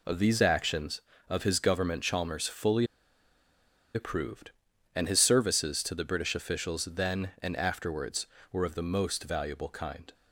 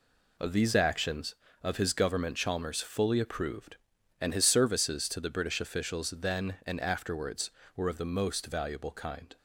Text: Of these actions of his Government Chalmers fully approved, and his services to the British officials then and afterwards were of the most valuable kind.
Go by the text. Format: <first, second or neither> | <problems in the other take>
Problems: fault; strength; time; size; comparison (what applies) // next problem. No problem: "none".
second | pauses between "fully" and "approved"; at 2.8 s; 1.0 s long